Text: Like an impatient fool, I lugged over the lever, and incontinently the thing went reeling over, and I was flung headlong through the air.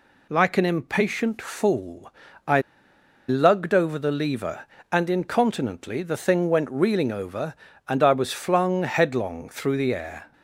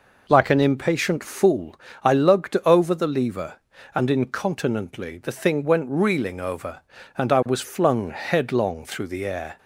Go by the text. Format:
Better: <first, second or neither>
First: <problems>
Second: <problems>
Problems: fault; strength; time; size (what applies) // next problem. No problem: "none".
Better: second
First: pauses between "I" and "lugged"; noticeable; at 2.6 s; 0.66 s long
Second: none